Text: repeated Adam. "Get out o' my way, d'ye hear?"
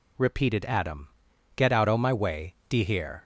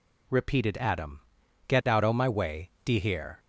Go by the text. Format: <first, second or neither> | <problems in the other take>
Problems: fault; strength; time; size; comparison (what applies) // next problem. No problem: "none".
neither | none